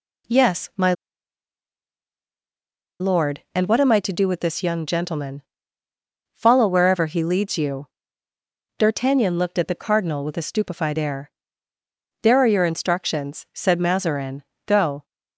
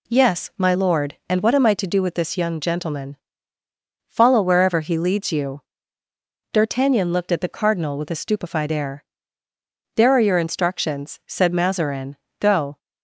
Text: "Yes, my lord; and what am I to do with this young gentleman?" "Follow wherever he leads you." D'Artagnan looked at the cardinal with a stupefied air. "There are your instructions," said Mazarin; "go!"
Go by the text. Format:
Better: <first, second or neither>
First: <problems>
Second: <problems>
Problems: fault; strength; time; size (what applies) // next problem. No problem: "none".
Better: second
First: pauses between "my" and "lord"; strong; at 0.9 s; 2.0 s long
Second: none